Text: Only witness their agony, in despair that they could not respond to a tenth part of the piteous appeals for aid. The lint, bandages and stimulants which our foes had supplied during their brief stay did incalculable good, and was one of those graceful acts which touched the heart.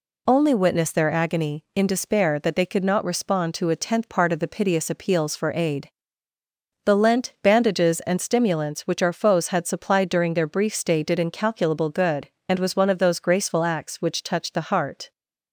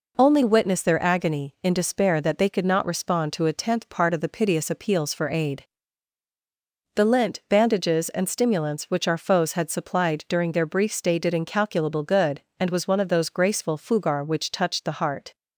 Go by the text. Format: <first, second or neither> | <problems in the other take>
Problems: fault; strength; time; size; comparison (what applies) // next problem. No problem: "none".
first | says "fugar" for "acts"; at 13.7 s